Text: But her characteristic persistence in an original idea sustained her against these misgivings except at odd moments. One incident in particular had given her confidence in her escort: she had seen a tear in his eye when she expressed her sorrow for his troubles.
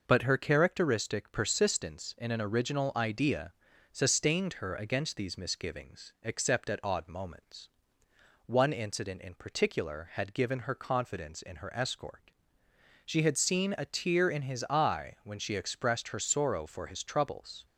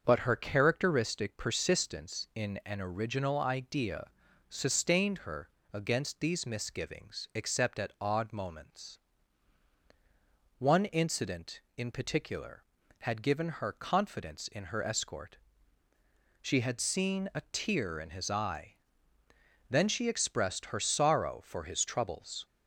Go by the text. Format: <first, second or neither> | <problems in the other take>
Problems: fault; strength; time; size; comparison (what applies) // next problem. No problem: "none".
first | starts louder than the rest; until 1.0 s; 6.5 dB // pauses between "idea" and "sustained"; at 4.0 s; 0.44 s long; also in the first // pauses between "her" and "against"; slight; at 5.4 s; 0.24 s long // says "then" for "when"; at 19.6 s